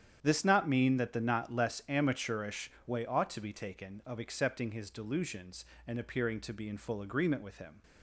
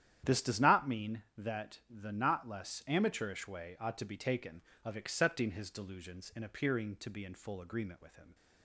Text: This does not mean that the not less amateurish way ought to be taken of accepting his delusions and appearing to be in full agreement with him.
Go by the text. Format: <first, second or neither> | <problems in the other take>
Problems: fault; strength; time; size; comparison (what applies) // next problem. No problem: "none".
second | starts louder than the rest; strong; until 1.2 s; 9 dB; strong in the second // skips "does"; at 0.4 s // pauses between "amateurish" and "way"; slight; at 2.7 s; 0.16 s long